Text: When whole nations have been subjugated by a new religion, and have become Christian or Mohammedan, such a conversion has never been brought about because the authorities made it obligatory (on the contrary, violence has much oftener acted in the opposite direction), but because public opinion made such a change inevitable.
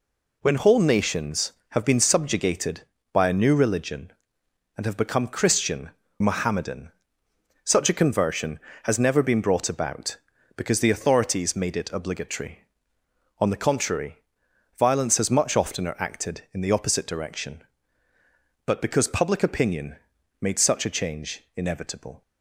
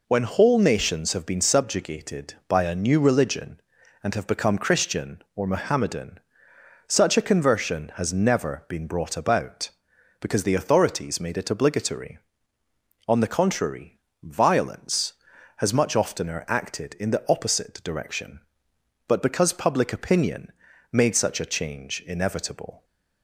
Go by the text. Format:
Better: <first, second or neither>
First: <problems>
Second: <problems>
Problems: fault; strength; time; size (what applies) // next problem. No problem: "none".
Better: second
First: skips "or"; at 6.0 s // pauses between "opinion" and "made"; noticeable; at 19.9 s; 0.46 s long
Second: pauses between "opinion" and "made"; at 20.5 s; 0.40 s long